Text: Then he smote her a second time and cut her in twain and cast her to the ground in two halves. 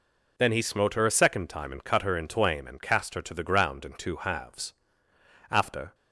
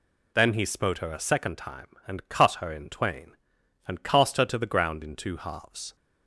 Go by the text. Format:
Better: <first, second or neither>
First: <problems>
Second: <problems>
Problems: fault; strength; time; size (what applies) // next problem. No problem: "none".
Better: second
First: goes on to say "After"; slight; from 5.5 s on; 0.44 s long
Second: none